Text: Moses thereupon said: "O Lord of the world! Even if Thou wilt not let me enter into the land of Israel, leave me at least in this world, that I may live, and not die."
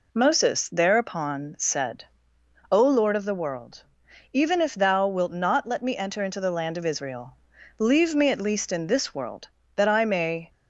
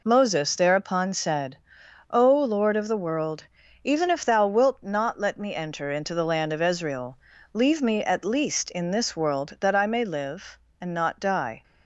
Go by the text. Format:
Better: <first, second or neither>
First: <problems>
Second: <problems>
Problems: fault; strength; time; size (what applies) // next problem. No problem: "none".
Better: second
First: stops before "live and not die"; at 10.4 s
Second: none